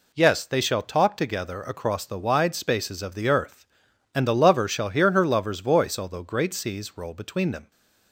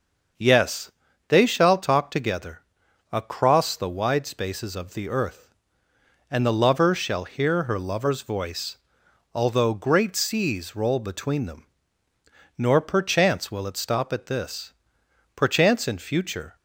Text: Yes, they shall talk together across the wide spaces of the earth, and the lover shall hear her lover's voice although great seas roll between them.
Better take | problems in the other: first | starts louder than the rest; until 1.7 s; 6.5 dB // pauses between "together" and "across"; noticeable; at 2.6 s; 0.50 s long // pauses between "voice" and "although"; noticeable; at 8.7 s; 0.56 s long // goes on to say "Nor perchance will it stop at this perchance in future"; strong; from 12.5 s on; 3.9 s long

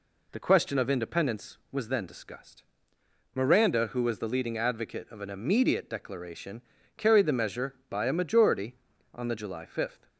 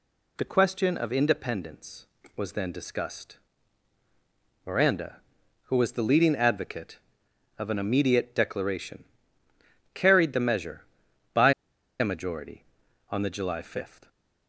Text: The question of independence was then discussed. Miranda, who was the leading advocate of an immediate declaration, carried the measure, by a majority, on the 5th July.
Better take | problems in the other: first | pauses between "by" and "a"; noticeable; at 11.5 s; 0.48 s long

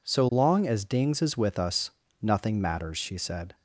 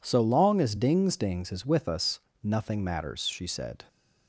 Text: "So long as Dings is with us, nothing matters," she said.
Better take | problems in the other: first | says "Dings" twice; at 1.1 s

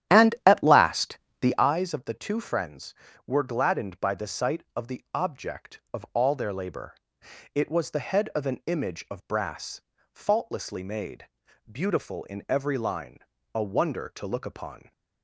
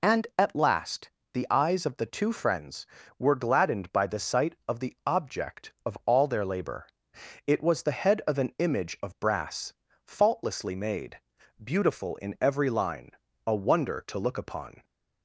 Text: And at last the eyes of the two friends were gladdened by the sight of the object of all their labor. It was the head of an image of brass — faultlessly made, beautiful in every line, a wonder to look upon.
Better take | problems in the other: second | starts louder than the rest; strong; until 1.7 s; 11 dB // pauses between "last" and "the"; slight; at 1.1 s; 0.24 s long; slight in the second

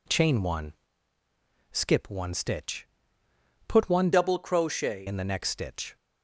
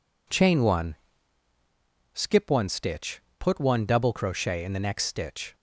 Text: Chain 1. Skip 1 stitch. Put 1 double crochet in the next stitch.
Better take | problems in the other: second | changes voice from "double" to "crochet"; from 4.1 to 5.0 s; 0.9 s long

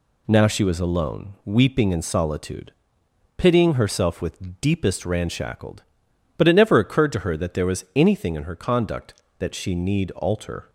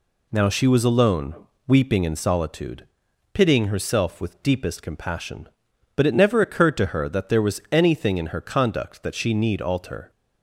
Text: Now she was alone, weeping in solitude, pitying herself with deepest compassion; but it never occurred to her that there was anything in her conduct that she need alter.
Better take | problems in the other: second | says "ranshackled" for "compassion"; at 5.0 s

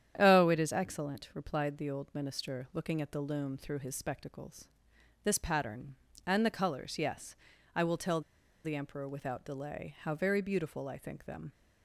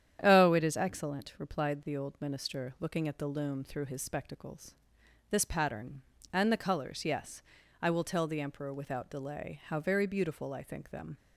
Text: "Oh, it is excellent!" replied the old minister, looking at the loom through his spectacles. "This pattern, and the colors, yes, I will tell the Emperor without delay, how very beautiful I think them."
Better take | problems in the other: second | starts louder than the rest; strong; until 1.1 s; 9.5 dB; strong in the second // pauses between "tell" and "the"; at 8.2 s; 0.42 s long

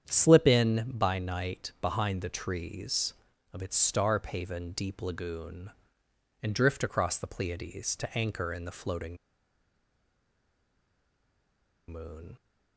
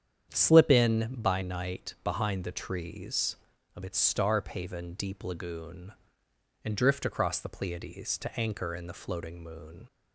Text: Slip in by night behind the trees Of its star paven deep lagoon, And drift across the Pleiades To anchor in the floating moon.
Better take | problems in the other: second | starts louder than the rest; strong; until 1.0 s; 8.5 dB; strong in the second // pauses between "floating" and "moon"; strong; at 9.1 s; 2.7 s long

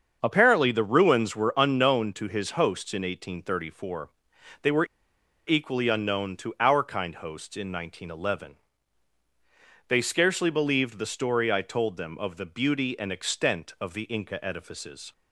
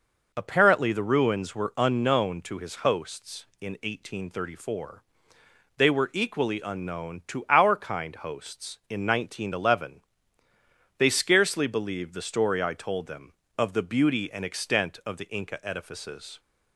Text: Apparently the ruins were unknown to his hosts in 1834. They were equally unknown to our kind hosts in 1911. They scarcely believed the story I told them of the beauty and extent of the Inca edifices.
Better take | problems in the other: second | starts louder than the rest; until 1.2 s; 7 dB // pauses between "were" and "equally"; noticeable; at 4.8 s; 0.61 s long

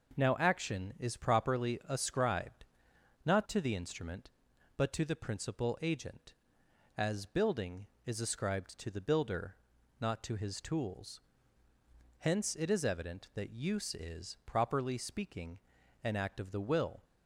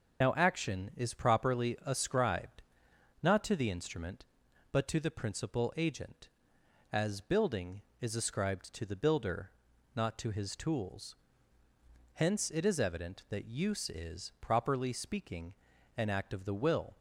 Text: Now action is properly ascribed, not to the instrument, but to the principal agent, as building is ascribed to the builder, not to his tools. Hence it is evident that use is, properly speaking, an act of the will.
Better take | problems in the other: first | loses the start of "Now"; at 0.2 s; 120 ms // starts louder than the rest; until 1.3 s; 6.5 dB

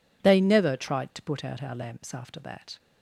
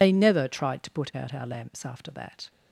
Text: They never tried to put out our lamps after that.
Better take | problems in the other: first | loses the start of "They"; at 0.0 s; 75 ms

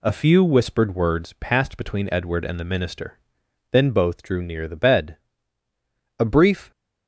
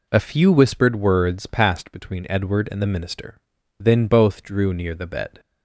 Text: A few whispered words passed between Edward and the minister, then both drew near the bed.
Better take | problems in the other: second | goes on to say "A brief"; from 6.1 s on; 0.52 s long

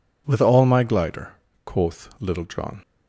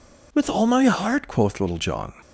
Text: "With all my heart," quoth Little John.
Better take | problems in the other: second | says "glider" for "heart"; at 0.8 s

